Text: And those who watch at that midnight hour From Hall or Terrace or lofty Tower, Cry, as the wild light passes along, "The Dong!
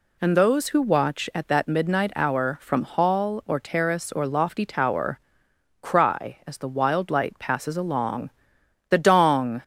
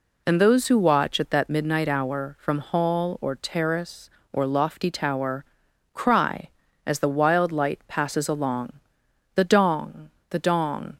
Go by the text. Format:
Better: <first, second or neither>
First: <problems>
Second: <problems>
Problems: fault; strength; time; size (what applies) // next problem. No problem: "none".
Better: first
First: none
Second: goes on to say "the Dong"; noticeable; from 10.2 s on; 0.68 s long